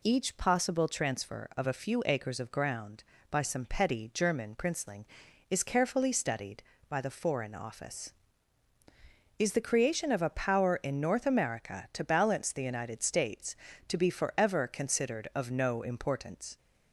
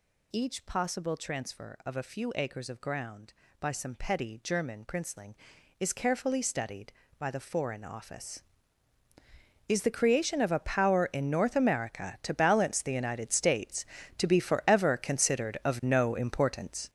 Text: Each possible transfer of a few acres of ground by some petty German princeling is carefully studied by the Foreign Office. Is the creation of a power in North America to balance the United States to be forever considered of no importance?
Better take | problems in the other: first | gets louder; strong; throughout; 9.5 dB

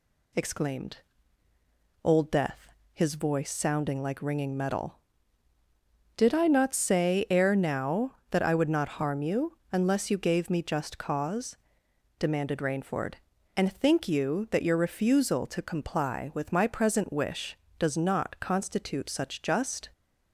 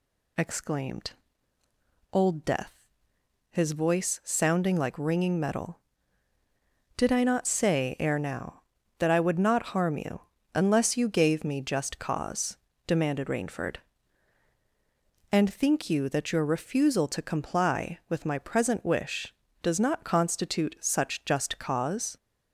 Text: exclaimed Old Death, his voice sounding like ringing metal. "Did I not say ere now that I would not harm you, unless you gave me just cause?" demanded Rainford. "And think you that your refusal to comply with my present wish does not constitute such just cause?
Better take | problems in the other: second | pauses between "exclaimed" and "Old"; at 0.9 s; 1.0 s long; also in the second // stops before "cause"; at 19.9 s

